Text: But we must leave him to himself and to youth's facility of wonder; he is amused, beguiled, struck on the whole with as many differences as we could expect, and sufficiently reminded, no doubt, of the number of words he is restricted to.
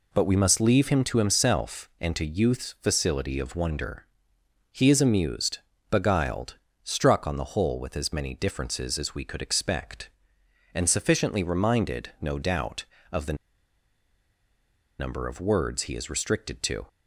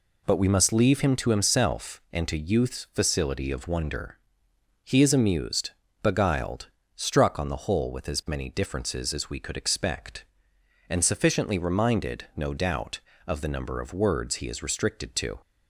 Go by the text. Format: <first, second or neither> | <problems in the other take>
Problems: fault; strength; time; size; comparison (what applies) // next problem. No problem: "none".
second | pauses between "the" and "number"; strong; at 13.3 s; 1.6 s long